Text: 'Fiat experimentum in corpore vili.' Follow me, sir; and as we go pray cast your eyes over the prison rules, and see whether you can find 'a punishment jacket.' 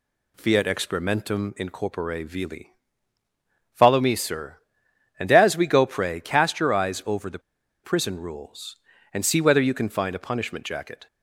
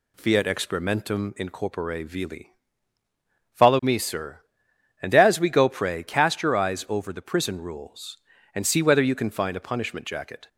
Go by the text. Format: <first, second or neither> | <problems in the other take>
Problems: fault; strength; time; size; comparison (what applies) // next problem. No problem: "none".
second | pauses between "the" and "prison"; at 7.3 s; 0.44 s long